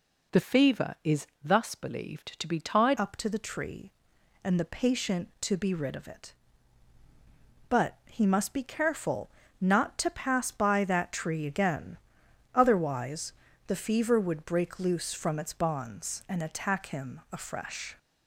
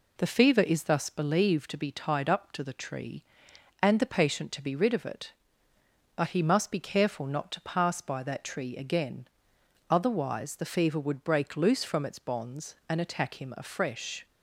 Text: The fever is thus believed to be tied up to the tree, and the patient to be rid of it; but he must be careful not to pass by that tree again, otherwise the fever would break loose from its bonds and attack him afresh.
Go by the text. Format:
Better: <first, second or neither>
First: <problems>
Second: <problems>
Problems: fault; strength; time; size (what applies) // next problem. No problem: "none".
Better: second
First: pauses between "is" and "thus"; slight; at 1.2 s; 0.18 s long // changes voice at "up"; from 2.9 s on; 15.0 s long // pauses between "careful" and "not"; slight; at 9.2 s; 0.30 s long // pauses between "otherwise" and "the"; slight; at 13.3 s; 0.32 s long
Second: none